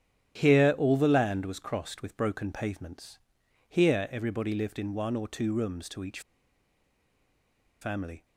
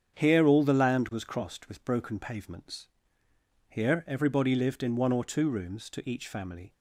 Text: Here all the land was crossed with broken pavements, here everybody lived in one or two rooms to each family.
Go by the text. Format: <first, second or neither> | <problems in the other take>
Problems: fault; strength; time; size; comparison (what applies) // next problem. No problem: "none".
second | starts louder than the rest; strong; until 1.4 s; 11 dB; strong in the second // pauses between "each" and "family"; strong; at 6.2 s; 1.6 s long